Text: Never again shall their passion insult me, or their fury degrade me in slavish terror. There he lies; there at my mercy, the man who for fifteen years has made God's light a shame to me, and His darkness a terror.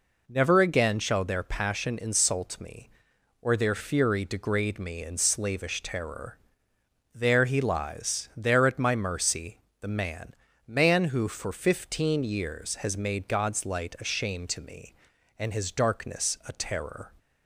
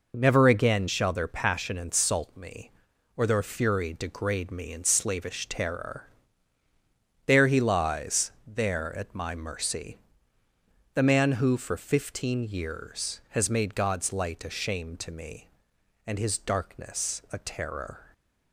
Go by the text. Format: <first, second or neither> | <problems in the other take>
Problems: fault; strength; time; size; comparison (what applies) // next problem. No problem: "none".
second | says "man" twice; at 10.6 s